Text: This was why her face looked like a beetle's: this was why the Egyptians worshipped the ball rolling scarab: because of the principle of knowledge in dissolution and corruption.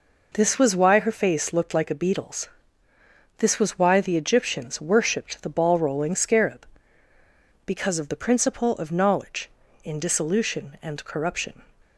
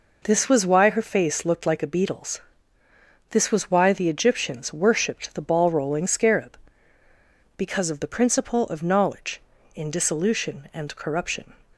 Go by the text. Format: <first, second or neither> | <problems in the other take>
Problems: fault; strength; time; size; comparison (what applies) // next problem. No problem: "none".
neither | none